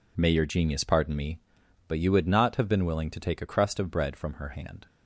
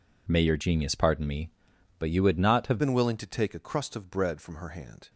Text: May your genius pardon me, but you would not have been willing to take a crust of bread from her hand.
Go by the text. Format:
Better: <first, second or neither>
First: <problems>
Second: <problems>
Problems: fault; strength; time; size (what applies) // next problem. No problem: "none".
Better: first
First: none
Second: changes voice at "been"; from 2.7 s on; 2.3 s long